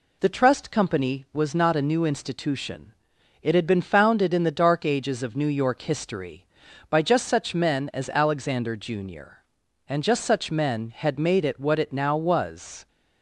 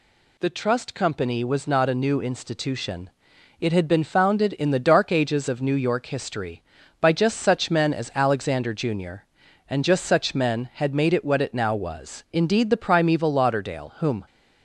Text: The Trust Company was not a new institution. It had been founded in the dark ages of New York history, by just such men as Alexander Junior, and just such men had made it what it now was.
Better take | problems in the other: first | goes on to say "Indeed the primeval Lauderdale whom"; strong; from 12.3 s on; 1.9 s long

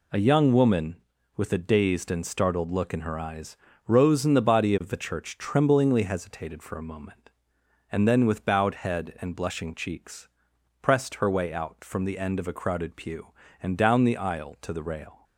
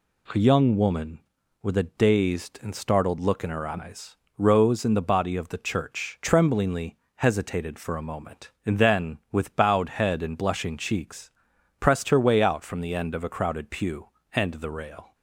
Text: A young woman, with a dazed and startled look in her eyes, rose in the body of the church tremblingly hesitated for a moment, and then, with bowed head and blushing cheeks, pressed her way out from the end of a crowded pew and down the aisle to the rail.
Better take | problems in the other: first | pauses between "tremblingly" and "hesitated"; slight; at 6.9 s; 0.20 s long // skips "down the aisle to"; at 14.5 s

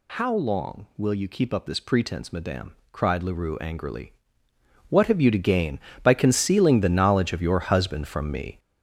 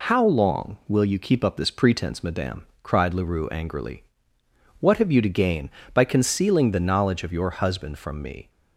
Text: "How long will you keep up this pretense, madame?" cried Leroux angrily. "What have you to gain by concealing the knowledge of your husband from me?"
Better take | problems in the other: second | gets louder; throughout; 7 dB

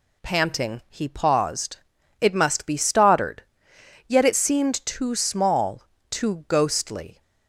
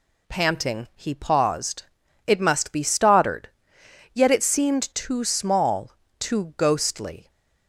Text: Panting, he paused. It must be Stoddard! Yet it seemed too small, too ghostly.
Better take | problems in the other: neither | none

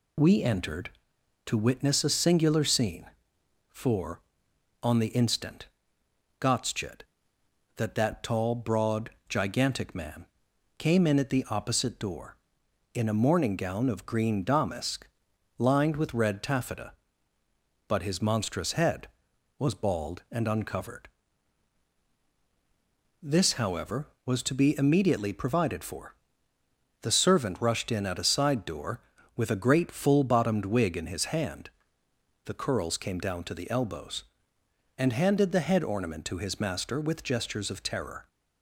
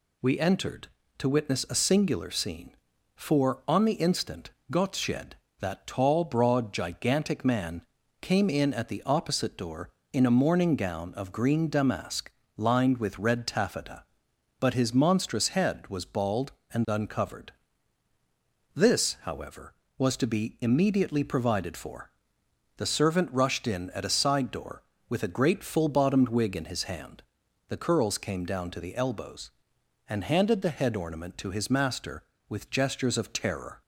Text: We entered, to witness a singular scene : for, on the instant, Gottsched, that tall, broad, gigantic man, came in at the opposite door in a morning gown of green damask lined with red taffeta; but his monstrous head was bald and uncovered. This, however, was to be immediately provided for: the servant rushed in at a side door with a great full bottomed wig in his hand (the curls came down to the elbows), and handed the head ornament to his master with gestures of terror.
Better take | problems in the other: second | says "that" twice; at 7.9 s // pauses between "damask" and "lined"; noticeable; at 15.0 s; 0.50 s long; slight in the second

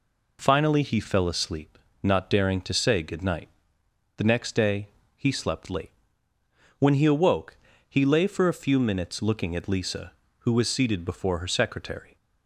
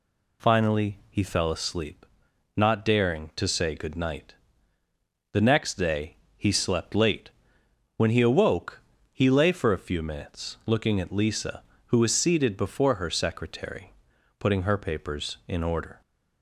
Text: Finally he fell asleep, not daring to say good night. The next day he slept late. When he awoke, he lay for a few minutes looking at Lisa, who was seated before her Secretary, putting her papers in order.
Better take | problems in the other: second | pauses between "day" and "he"; slight; at 4.8 s; 0.26 s long; slight in the second // stops before "putting her papers in order"; at 12.1 s

